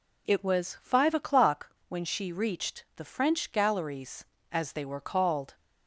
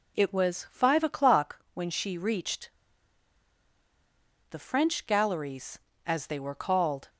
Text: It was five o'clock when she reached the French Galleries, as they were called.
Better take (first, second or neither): first